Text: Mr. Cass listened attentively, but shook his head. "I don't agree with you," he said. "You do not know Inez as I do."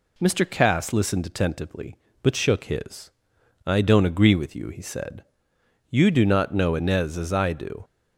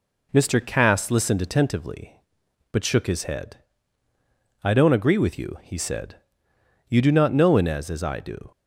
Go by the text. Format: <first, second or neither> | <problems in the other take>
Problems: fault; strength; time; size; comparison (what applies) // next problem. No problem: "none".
second | skips "head"; at 3.3 s